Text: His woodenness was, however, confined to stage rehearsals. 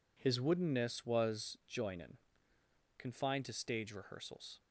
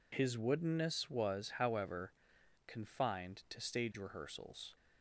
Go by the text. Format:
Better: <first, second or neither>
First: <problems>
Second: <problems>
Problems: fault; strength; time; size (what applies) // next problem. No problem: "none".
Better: second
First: says "joinin" for "however"; at 1.6 s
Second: none